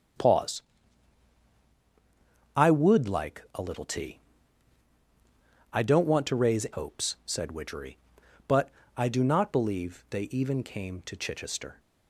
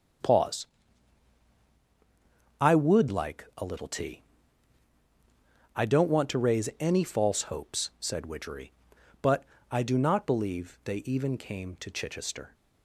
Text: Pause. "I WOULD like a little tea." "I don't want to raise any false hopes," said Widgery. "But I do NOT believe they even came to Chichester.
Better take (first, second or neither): second